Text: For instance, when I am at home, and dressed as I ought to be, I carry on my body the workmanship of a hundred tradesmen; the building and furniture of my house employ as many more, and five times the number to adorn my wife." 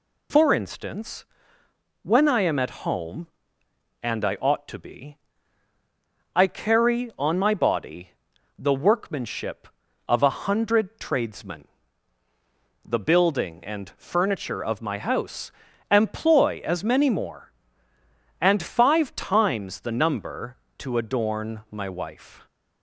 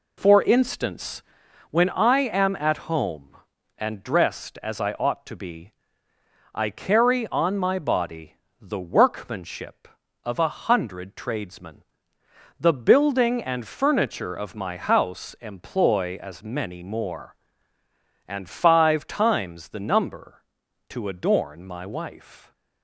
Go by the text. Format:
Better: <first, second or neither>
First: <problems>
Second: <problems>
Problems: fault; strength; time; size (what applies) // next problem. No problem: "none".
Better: second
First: skips "dressed as"; at 4.2 s // pauses between "body" and "the"; noticeable; at 8.1 s; 0.46 s long // pauses between "house" and "employ"; at 15.4 s; 0.40 s long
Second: pauses between "body" and "the"; slight; at 8.3 s; 0.26 s long